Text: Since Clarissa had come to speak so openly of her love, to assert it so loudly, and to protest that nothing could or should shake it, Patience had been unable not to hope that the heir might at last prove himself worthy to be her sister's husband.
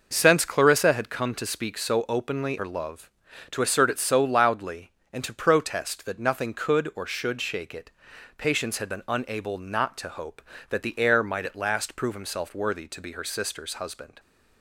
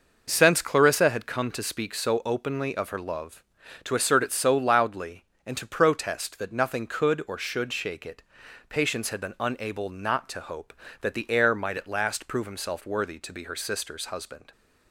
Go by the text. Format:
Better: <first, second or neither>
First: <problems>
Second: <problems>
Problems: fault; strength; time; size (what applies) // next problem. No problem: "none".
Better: second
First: skips "of"; at 2.5 s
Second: none